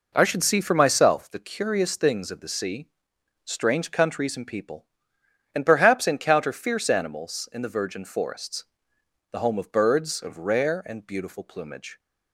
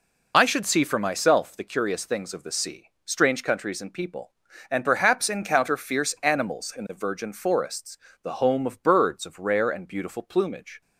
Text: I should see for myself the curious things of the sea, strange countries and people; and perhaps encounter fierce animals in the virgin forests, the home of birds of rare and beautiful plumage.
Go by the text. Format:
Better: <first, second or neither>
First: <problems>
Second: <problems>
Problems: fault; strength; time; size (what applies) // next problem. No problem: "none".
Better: first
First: none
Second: loses the start of "I"; at 0.3 s; 55 ms